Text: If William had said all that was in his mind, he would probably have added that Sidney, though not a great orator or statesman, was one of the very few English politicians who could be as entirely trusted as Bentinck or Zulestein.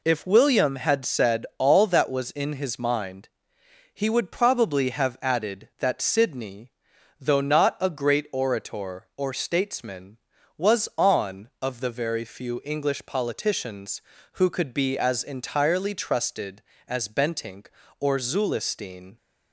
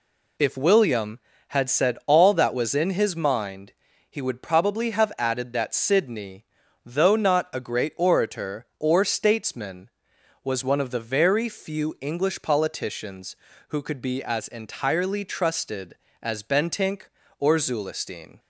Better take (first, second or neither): second